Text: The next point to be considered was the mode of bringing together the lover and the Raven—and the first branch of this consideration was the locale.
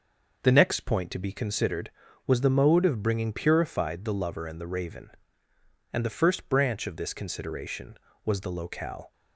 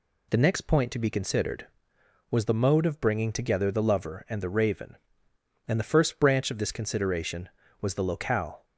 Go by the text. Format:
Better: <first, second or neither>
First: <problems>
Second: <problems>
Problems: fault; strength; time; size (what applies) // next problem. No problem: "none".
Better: second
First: says "purified" for "together"; at 3.3 s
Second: none